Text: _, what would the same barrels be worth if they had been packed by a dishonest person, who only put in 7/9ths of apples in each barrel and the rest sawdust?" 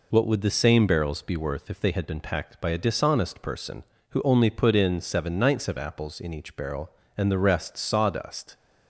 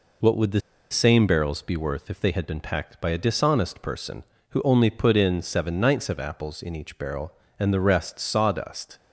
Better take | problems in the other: first | pauses between "the" and "same"; slight; at 0.5 s; 0.31 s long

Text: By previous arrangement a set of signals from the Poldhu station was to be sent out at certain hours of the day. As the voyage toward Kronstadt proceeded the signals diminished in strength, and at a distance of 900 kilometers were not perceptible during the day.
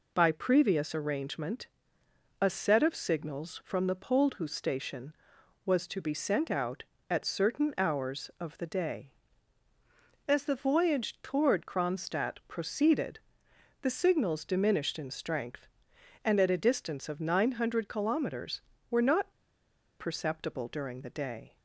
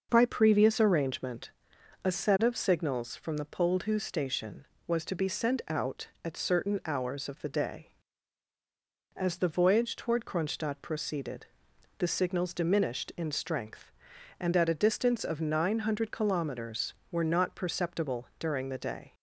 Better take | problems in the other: second | pauses between "arrangement" and "a"; noticeable; at 1.6 s; 0.74 s long; noticeable in the second // pauses between "proceeded" and "the"; noticeable; at 13.1 s; 0.62 s long; noticeable in the second // pauses between "not" and "perceptible"; noticeable; at 19.2 s; 0.69 s long

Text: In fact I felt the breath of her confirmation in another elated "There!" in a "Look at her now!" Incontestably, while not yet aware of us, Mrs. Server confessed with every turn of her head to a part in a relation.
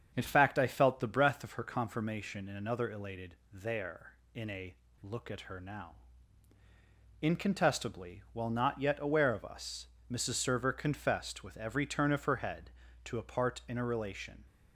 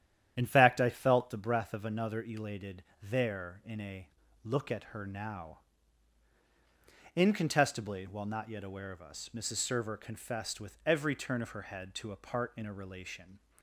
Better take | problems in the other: first | starts louder than the rest; strong; until 1.3 s; 10.5 dB; strong in the first // skips "her confirmation in"; at 1.8 s // pauses between "elated" and "There"; slight; at 2.8 s; 0.20 s long; slight in the first // pauses between "a" and "Look"; at 4.0 s; 0.38 s long; slight in the first

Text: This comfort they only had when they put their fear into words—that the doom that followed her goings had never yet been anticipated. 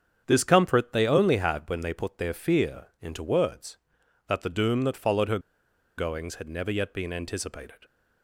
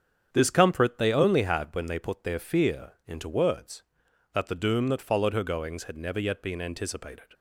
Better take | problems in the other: second | starts louder than the rest; strong; until 1.2 s; 8.5 dB; strong in the second // pauses between "fear" and "into"; slight; at 2.8 s; 0.16 s long; slight in the second // pauses between "her" and "goings"; noticeable; at 5.3 s; 0.59 s long

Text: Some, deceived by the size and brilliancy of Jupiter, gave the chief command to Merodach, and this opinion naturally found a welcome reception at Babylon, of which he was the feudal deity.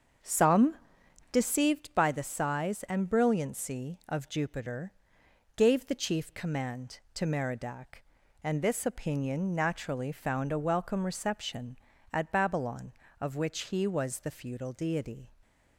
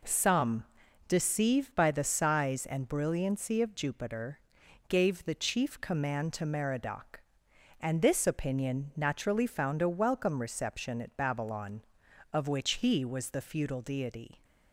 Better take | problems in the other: second | starts louder than the rest; until 1.7 s; 7 dB

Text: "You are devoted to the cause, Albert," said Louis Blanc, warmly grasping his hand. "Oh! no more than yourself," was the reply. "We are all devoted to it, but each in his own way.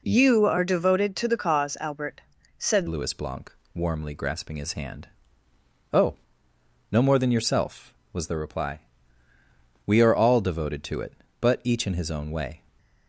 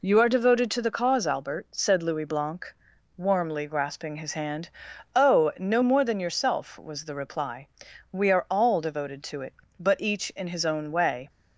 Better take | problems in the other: second | changes voice at "Louis"; from 2.8 s on; 9.8 s long

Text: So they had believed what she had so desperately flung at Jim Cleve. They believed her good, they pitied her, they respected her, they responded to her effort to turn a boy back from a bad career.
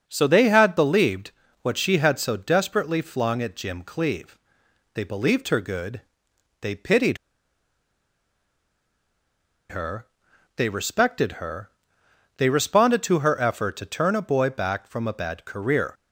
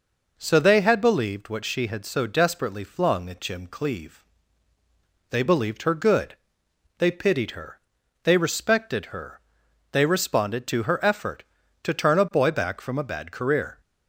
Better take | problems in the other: second | starts louder than the rest; until 1.0 s; 6.5 dB // pauses between "believed" and "what"; slight; at 1.3 s; 0.30 s long // pauses between "pitied" and "her"; strong; at 7.1 s; 2.5 s long

